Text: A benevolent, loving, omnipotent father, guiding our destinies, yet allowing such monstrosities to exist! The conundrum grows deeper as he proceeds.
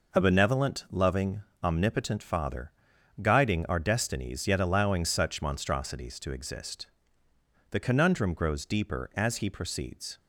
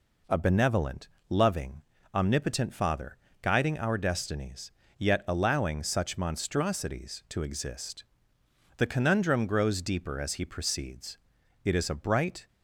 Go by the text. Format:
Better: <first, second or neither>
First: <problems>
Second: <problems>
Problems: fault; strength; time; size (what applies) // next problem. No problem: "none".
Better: first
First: none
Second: goes on to say "It is a bright"; noticeable; from 11.6 s on; 0.84 s long